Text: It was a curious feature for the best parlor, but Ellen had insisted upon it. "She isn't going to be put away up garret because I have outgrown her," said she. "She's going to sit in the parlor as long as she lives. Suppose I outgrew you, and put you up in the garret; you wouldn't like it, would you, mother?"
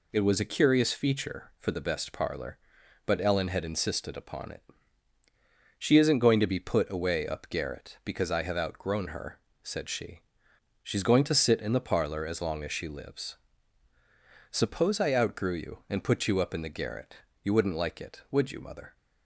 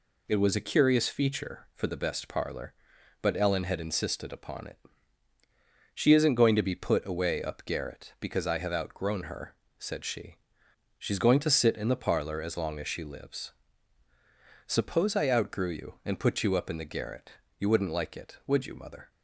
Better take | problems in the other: neither | none

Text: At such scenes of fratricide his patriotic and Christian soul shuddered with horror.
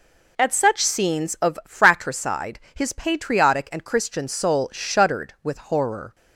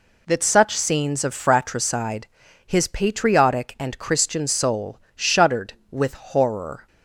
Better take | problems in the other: first | says "That" for "At"; at 0.2 s // pauses between "fratricide" and "his"; at 2.2 s; 0.40 s long; slight in the first // pauses between "soul" and "shuddered"; slight; at 4.9 s; 0.16 s long

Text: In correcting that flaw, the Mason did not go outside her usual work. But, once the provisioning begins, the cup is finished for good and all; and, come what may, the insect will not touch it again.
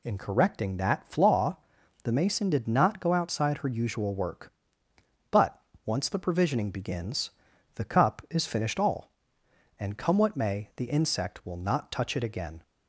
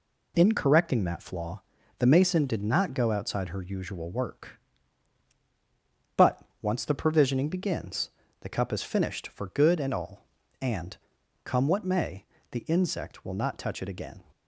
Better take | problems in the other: second | skips "for good and"; at 8.7 s

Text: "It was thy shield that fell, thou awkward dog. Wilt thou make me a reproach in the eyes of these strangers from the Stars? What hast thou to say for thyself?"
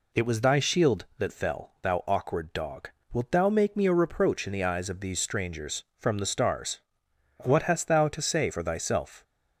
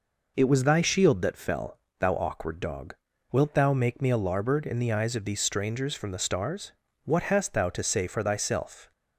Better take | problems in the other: first | says "larboard" for "reproach"; at 4.1 s

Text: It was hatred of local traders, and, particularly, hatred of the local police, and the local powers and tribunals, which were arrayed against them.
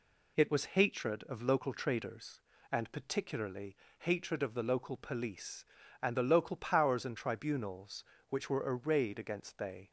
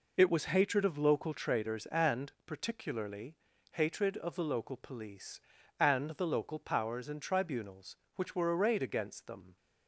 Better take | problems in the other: second | says "they" for "them"; at 9.5 s

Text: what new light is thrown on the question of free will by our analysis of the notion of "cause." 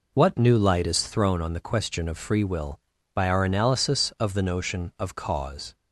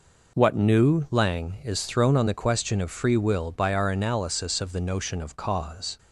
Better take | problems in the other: first | says "lang" for "light"; at 1.1 s

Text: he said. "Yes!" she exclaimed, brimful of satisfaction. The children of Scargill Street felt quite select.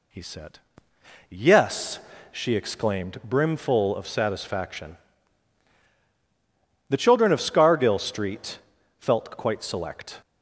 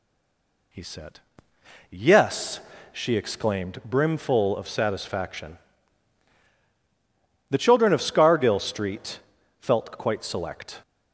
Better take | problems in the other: first | stays silent before the first word; slight; until 0.7 s; 0.7 s long // pauses between "Street" and "felt"; at 9.1 s; 0.42 s long; also in the first

